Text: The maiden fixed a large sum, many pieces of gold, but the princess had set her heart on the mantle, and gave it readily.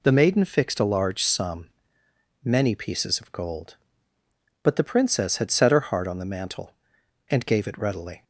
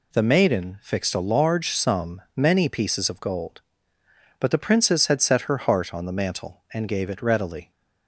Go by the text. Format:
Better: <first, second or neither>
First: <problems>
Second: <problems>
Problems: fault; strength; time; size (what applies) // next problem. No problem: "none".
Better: neither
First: none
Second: none